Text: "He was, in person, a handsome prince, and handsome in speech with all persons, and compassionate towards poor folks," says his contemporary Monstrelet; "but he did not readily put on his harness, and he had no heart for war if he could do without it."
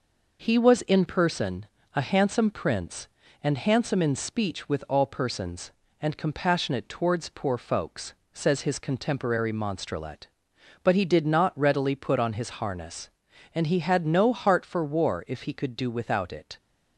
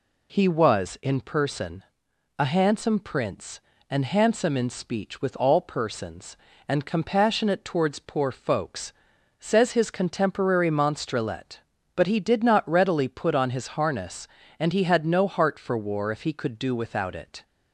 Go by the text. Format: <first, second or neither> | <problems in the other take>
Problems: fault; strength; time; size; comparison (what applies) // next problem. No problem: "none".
neither | none